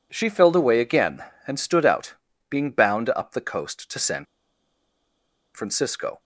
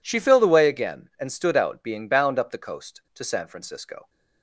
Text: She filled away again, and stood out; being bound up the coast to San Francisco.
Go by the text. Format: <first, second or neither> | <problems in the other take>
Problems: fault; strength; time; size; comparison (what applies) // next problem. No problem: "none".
second | pauses between "San" and "Francisco"; strong; at 4.2 s; 1.2 s long